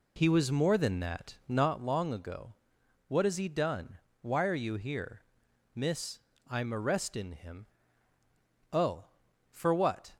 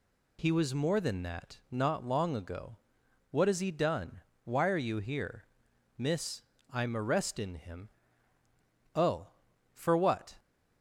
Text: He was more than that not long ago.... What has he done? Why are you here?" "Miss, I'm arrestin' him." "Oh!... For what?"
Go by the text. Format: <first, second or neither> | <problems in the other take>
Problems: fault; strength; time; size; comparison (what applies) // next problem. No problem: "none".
second | starts louder than the rest; slight; until 1.9 s; 2.5 dB